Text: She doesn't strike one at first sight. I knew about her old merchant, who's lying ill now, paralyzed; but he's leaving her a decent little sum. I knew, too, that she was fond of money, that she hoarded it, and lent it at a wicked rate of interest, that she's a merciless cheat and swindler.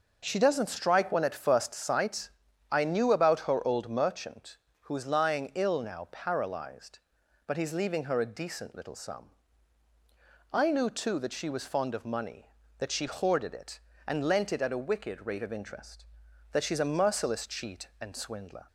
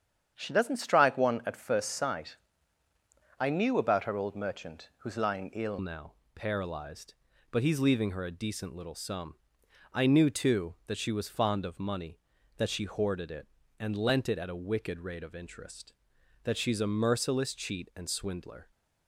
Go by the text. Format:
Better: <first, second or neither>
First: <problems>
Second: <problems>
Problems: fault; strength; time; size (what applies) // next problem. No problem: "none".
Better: first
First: none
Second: starts louder than the rest; strong; until 1.3 s; 8.5 dB // changes voice at "now"; from 5.7 s on; 13.0 s long